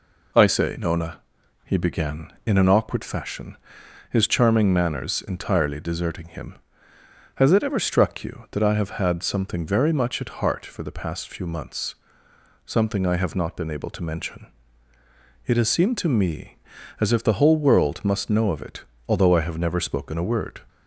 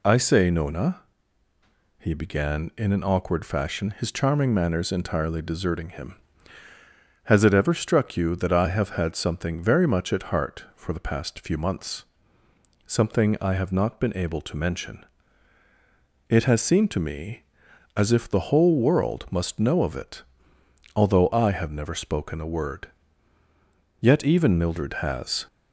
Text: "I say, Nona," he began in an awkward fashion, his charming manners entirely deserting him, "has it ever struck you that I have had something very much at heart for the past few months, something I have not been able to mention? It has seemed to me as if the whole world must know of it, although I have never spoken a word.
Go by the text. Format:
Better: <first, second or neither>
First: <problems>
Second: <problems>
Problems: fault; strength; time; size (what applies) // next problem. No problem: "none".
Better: first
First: none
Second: goes on to say "Yet even Mildred has"; from 24.0 s on; 1.4 s long